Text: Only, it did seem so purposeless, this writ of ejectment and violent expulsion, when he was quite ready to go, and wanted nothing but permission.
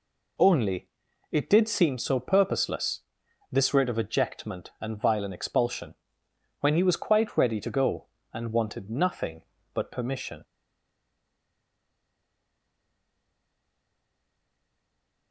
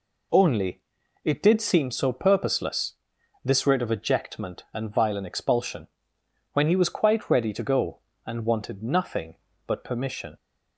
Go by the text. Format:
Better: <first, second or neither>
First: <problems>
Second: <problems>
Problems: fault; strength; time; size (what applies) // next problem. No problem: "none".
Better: second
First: stays silent after the last word; strong; from 10.4 s on; 4.9 s long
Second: none